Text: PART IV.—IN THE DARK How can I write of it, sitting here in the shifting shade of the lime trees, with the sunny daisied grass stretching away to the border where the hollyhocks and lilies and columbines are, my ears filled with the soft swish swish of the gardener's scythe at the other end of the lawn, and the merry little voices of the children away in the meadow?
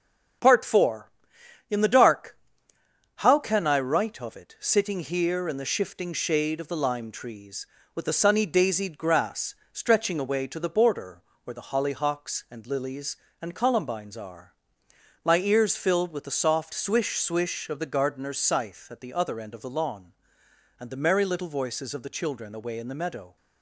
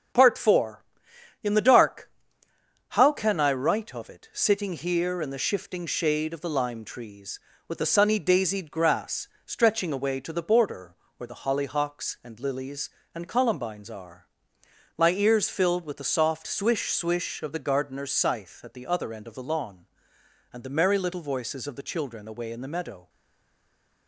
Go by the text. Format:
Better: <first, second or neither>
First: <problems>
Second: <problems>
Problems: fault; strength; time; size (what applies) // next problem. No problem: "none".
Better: first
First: starts louder than the rest; strong; until 2.0 s; 7 dB // pauses between "DARK" and "How"; noticeable; at 2.3 s; 0.78 s long // pauses between "grass" and "stretching"; slight; at 9.5 s; 0.18 s long // pauses between "border" and "where"; slight; at 11.2 s; 0.22 s long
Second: starts louder than the rest; strong; until 1.7 s; 7 dB // pauses between "DARK" and "How"; noticeable; at 2.1 s; 0.78 s long // pauses between "grass" and "stretching"; slight; at 9.2 s; 0.18 s long // pauses between "border" and "where"; slight; at 10.9 s; 0.22 s long // stays silent after the last word; from 23.0 s on; 1.0 s long